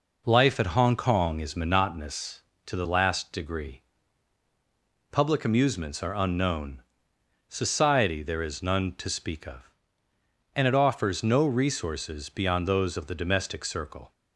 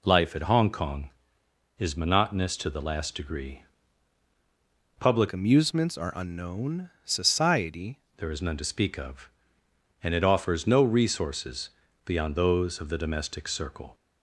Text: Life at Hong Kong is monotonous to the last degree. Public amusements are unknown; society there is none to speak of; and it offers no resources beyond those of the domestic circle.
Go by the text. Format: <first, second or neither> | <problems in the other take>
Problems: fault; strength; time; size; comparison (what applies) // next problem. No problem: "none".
first | changes voice from "amusements" to "society"; from 5.3 to 7.9 s; 2.6 s long // pauses between "resources" and "beyond"; slight; at 11.6 s; 0.36 s long